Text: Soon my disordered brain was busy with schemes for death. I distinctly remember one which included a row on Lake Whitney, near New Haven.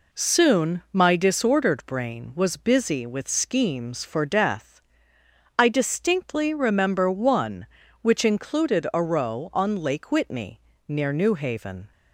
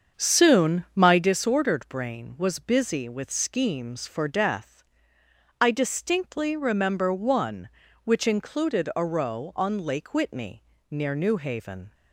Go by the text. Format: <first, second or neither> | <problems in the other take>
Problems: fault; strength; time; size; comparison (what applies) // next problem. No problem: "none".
first | starts louder than the rest; strong; until 1.3 s; 7 dB